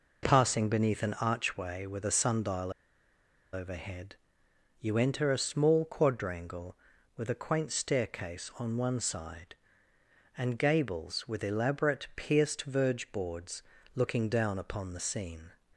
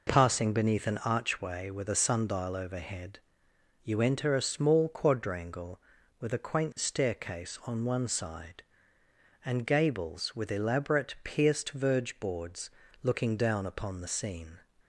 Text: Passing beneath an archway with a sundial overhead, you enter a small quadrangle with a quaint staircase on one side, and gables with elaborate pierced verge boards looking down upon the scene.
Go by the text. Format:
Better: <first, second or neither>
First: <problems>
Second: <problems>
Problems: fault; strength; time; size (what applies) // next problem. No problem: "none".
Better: second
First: pauses between "sundial" and "overhead"; noticeable; at 2.7 s; 0.81 s long // pauses between "boards" and "looking"; slight; at 13.6 s; 0.34 s long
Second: pauses between "boards" and "looking"; slight; at 12.6 s; 0.34 s long